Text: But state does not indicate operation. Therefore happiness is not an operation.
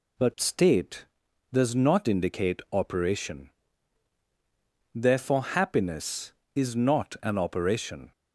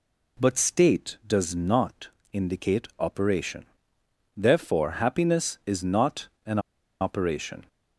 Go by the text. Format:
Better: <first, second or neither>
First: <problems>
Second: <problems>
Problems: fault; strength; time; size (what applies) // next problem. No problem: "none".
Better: first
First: none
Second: pauses between "not" and "indicate"; slight; at 2.0 s; 0.24 s long // pauses between "not" and "an"; slight; at 6.2 s; 0.18 s long // pauses between "an" and "operation"; at 6.5 s; 0.40 s long